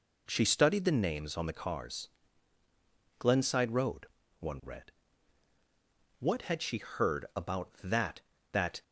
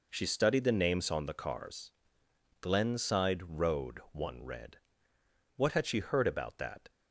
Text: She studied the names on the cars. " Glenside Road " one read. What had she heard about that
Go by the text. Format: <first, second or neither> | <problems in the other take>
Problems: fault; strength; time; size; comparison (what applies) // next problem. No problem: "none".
second | says "that" twice; at 8.5 s